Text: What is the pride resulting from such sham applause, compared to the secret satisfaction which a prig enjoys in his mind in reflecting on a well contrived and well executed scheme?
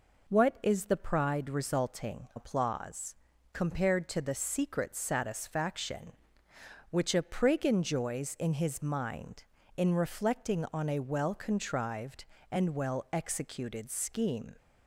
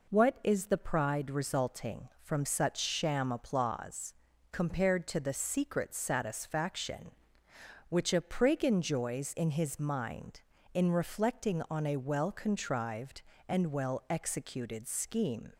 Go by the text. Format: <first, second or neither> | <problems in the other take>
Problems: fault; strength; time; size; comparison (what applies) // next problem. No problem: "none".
second | skips "from such sham"; at 2.3 s